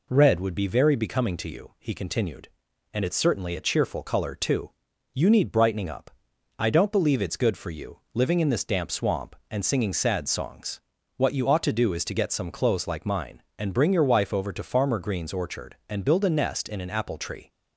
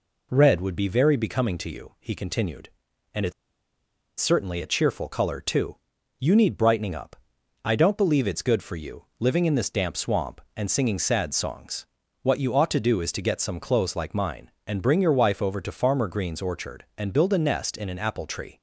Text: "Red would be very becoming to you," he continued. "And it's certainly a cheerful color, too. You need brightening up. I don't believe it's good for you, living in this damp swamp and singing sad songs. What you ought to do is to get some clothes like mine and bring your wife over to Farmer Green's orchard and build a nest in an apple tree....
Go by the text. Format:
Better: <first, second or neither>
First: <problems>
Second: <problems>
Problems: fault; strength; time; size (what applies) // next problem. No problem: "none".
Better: first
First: none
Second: pauses between "it's" and "certainly"; noticeable; at 3.3 s; 0.87 s long